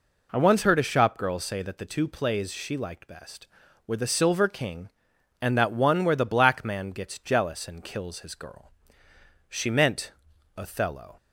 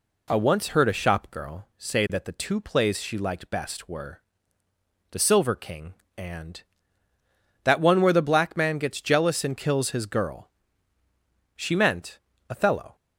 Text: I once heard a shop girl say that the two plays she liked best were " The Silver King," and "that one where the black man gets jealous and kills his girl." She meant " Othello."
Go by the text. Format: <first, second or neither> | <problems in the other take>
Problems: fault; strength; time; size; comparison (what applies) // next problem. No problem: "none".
neither | none